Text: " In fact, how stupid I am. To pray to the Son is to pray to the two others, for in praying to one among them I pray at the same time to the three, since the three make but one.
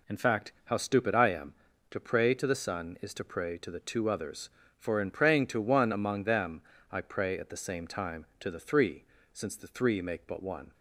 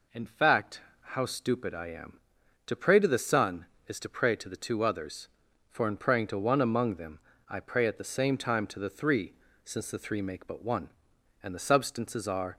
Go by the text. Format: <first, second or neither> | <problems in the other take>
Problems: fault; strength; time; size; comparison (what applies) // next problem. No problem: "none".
first | pauses between "them" and "I"; slight; at 7.1 s; 0.28 s long; slight in the first // goes on to say "And the Substances are"; noticeable; from 11.4 s on; 1.1 s long